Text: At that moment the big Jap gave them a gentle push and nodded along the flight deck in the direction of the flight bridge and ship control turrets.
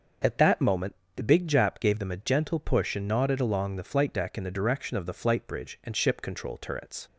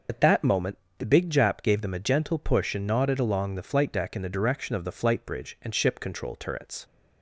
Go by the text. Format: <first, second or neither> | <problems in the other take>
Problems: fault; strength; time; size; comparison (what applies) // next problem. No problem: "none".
first | loses the start of "At"; at 0.0 s; 55 ms // pauses between "moment" and "the"; slight; at 0.7 s; 0.22 s long; slight in the first